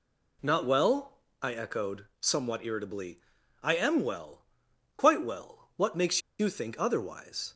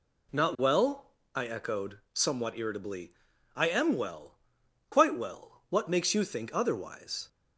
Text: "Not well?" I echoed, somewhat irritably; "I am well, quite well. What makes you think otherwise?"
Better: second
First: pauses between "makes" and "you"; slight; at 6.2 s; 0.18 s long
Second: none

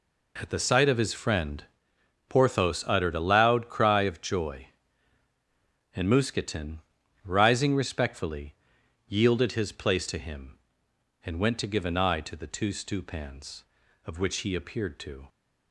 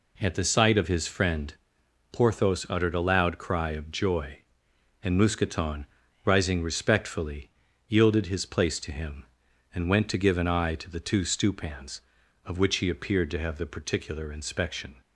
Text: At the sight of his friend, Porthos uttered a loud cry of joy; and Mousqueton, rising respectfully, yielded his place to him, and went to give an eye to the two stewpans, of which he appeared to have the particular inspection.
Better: second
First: stops before "have the particular inspection"; at 15.2 s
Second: none

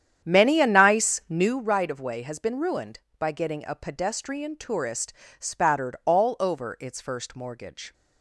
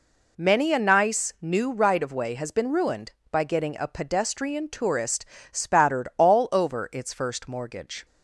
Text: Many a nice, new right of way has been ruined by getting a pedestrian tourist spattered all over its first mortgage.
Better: second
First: starts louder than the rest; strong; until 1.7 s; 9 dB // pauses between "tourist" and "spattered"; slight; at 5.1 s; 0.26 s long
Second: pauses between "tourist" and "spattered"; slight; at 5.2 s; 0.26 s long

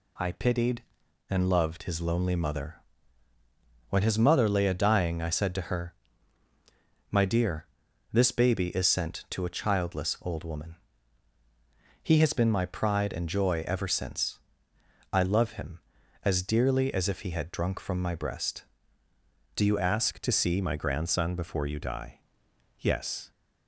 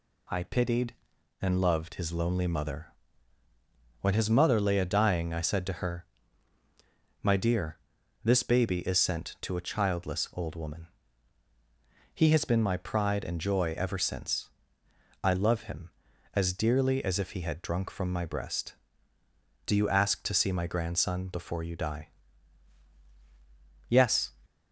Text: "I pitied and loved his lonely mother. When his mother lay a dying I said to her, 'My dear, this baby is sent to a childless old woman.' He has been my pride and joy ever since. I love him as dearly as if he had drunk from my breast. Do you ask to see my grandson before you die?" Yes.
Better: second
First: changes voice at "ask"; from 19.7 s on; 3.6 s long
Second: none

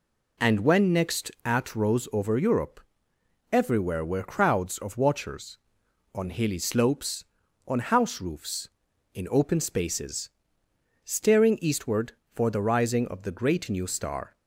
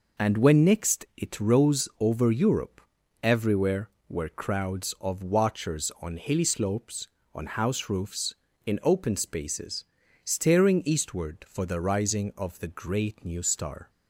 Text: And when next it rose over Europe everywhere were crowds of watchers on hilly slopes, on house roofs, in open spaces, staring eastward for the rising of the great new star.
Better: second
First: says "at" for "it"; at 1.4 s // pauses between "Europe" and "everywhere"; noticeable; at 2.8 s; 0.70 s long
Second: pauses between "Europe" and "everywhere"; at 2.8 s; 0.42 s long

